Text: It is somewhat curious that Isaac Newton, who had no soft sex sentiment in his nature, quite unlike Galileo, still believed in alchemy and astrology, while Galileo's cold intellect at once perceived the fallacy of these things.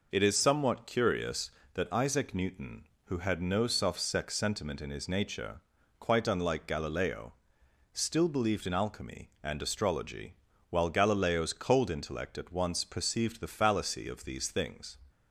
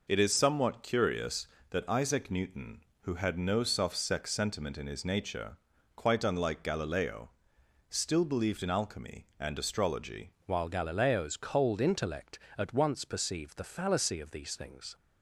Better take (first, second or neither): first